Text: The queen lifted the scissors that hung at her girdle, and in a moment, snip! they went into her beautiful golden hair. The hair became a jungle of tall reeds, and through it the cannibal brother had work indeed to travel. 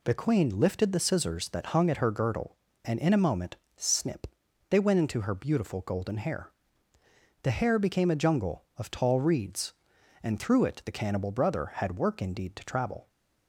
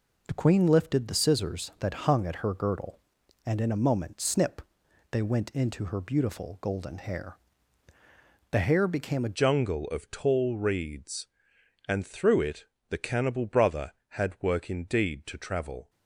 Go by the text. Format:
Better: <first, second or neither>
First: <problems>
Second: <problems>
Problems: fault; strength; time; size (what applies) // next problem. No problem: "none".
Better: first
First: none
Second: changes voice at "jungle"; from 9.3 s on; 6.5 s long // pauses between "it" and "the"; slight; at 12.6 s; 0.24 s long